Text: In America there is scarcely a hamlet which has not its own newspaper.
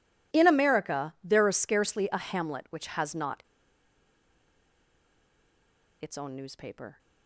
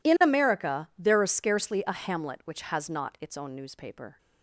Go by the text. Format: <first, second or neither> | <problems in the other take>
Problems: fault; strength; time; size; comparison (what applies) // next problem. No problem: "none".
second | pauses between "not" and "its"; strong; at 3.4 s; 2.5 s long